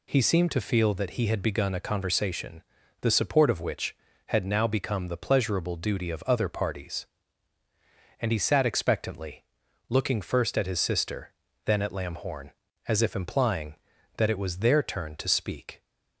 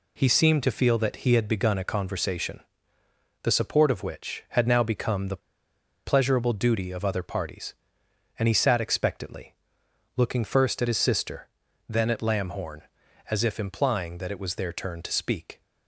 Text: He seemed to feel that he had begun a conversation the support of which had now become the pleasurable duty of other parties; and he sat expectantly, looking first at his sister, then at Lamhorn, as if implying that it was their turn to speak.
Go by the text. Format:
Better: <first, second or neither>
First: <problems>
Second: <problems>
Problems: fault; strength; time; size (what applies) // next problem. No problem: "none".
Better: first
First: pauses between "conversation" and "the"; at 2.6 s; 0.38 s long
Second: pauses between "conversation" and "the"; noticeable; at 2.6 s; 0.82 s long // pauses between "the" and "pleasurable"; noticeable; at 5.4 s; 0.66 s long